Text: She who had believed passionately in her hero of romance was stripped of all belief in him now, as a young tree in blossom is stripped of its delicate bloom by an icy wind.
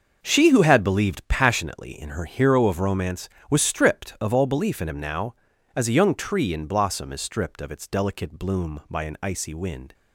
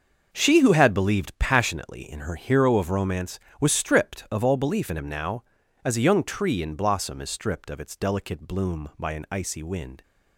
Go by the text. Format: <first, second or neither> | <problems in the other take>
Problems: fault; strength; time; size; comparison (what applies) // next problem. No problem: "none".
neither | starts louder than the rest; the same in both